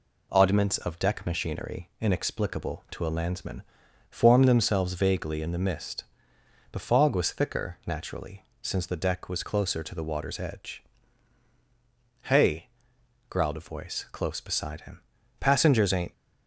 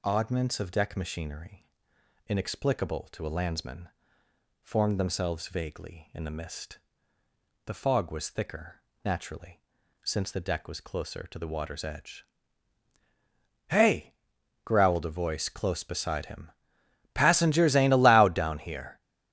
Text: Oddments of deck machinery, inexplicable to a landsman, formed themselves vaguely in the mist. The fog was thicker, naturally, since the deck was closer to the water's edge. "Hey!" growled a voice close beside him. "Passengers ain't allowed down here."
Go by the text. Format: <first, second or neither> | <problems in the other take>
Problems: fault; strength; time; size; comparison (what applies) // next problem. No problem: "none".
second | stops before "allowed down here"; at 16.1 s